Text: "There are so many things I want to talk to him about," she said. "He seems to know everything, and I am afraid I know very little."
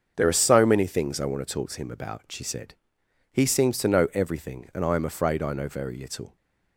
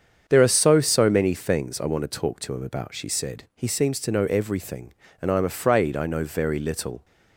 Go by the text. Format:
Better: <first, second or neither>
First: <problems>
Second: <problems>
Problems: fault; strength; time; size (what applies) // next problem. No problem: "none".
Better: first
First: starts louder than the rest; until 1.1 s; 7 dB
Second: starts louder than the rest; strong; until 1.2 s; 7.5 dB // says "so" twice; at 0.8 s